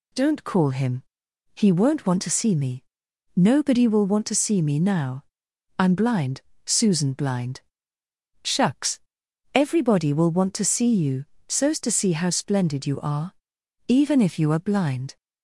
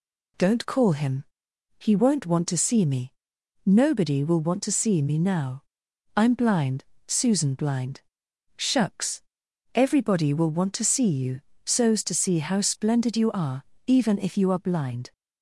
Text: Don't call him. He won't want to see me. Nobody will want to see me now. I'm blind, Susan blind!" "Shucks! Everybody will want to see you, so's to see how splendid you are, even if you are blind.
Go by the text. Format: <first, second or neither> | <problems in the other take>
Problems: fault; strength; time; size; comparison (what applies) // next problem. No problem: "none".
neither | none